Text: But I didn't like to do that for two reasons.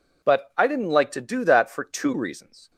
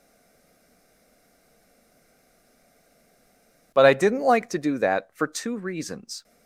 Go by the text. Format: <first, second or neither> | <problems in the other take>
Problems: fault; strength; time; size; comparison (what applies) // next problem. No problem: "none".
first | stays silent before the first word; strong; until 3.7 s; 3.7 s long